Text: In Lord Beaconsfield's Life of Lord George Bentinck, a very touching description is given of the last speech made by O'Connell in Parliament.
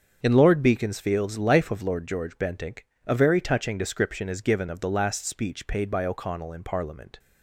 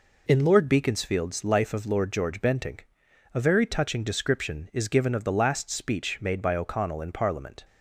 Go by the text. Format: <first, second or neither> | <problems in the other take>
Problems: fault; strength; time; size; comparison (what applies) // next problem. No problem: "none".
second | starts louder than the rest; until 1.2 s; 6.5 dB // says "paid" for "made"; at 5.6 s